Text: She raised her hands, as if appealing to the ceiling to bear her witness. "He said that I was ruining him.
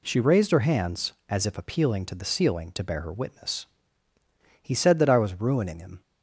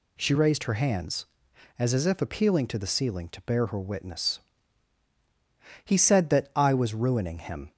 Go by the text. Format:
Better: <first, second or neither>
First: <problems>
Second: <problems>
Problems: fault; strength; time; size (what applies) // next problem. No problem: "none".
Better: first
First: none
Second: says "as" twice; at 1.9 s